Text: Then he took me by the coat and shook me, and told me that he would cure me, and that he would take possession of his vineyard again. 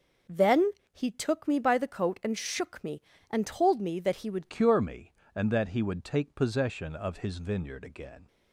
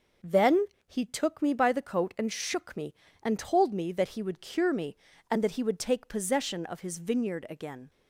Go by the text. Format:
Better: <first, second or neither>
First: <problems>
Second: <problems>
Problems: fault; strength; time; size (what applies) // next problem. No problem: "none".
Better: second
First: pauses between "Then" and "he"; slight; at 0.7 s; 0.20 s long // changes voice at "cure"; from 4.4 s on; 3.8 s long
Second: pauses between "Then" and "he"; slight; at 0.6 s; 0.20 s long